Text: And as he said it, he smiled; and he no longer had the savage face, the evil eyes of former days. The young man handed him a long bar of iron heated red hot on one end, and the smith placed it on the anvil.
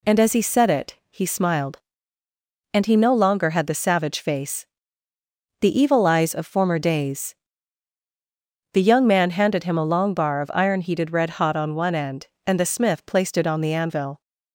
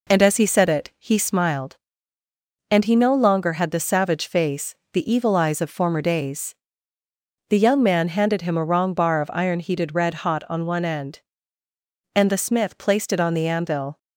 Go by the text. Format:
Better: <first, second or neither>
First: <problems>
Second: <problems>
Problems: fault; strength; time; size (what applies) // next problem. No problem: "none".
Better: first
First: none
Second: says "wrong" for "long"; at 8.6 s